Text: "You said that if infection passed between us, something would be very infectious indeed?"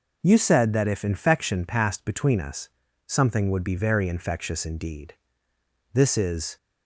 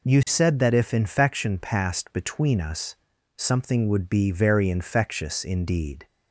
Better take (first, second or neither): second